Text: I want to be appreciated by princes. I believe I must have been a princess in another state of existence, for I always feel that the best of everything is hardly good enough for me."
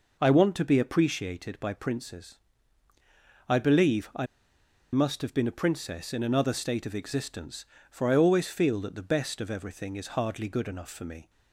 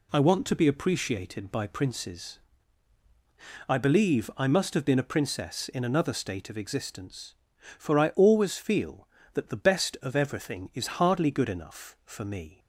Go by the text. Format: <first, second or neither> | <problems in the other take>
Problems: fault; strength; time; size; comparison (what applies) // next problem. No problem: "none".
second | pauses between "I" and "must"; noticeable; at 4.2 s; 0.67 s long